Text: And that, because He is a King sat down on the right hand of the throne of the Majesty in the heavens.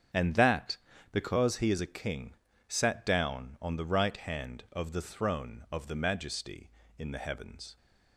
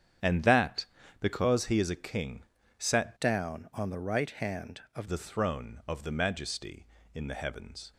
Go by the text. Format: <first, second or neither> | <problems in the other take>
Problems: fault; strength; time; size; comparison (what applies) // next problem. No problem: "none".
first | starts louder than the rest; strong; until 1.5 s; 8.5 dB; strong in the first // pauses between "King" and "sat"; slight; at 2.4 s; 0.36 s long; slight in the first // changes voice from "down" to "of"; from 3.1 to 5.0 s; 1.9 s long